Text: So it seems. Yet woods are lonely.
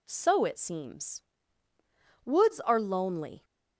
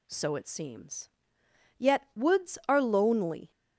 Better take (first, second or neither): second